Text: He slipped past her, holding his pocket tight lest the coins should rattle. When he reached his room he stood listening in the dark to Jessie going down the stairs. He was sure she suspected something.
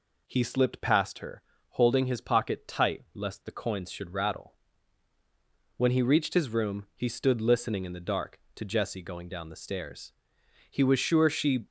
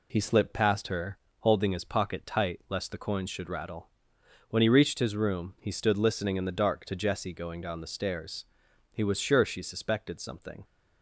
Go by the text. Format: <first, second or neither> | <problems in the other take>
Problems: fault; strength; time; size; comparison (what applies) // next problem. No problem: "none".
second | stops before "suspected something"; at 11.6 s